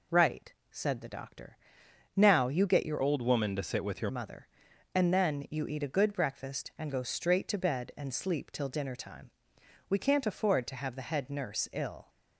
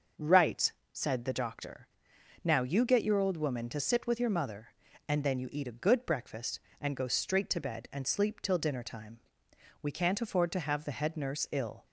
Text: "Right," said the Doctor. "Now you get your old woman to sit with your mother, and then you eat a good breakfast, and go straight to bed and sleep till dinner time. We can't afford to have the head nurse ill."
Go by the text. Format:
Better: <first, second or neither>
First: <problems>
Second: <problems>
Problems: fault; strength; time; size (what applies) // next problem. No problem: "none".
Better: second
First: changes voice from "old" to "your"; from 3.0 to 4.0 s; 1.0 s long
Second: none